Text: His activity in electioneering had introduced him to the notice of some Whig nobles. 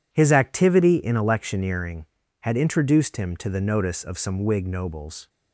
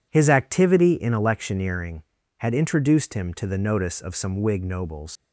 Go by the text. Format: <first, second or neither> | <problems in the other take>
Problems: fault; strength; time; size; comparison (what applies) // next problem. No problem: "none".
first | leaves "nobles" unfinished; at 5.1 s; 110 ms